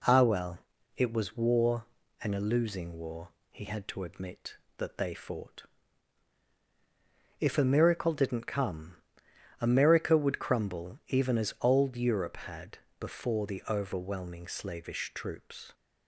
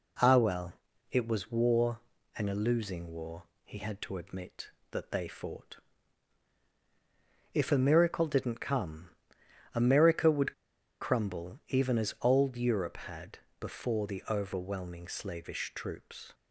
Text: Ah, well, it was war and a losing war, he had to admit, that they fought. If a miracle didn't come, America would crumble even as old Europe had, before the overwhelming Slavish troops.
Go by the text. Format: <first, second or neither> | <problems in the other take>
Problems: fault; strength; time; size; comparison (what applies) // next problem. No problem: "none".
first | pauses between "would" and "crumble"; noticeable; at 10.5 s; 0.48 s long